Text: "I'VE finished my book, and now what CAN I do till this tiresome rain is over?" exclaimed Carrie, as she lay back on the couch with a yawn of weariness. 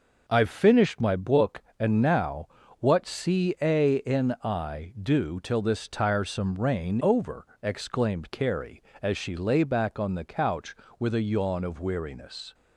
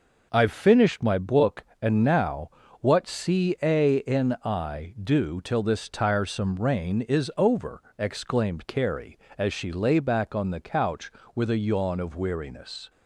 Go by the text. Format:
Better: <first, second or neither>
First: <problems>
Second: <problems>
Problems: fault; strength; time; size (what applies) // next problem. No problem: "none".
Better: second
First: pauses between "now" and "what"; slight; at 2.4 s; 0.32 s long // skips "is"; at 7.0 s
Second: pauses between "now" and "what"; slight; at 2.5 s; 0.30 s long